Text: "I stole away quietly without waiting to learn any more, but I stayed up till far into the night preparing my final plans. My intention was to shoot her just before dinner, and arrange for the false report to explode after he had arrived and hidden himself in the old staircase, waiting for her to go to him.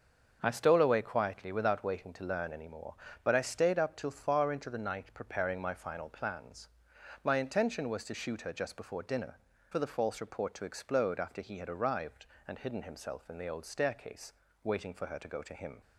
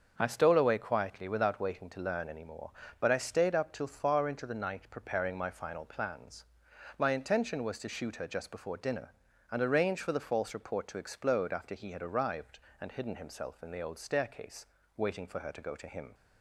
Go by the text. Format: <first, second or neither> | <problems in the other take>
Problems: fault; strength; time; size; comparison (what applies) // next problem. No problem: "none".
second | starts louder than the rest; until 1.4 s; 6.5 dB; also in the second // skips "and arrange"; at 9.5 s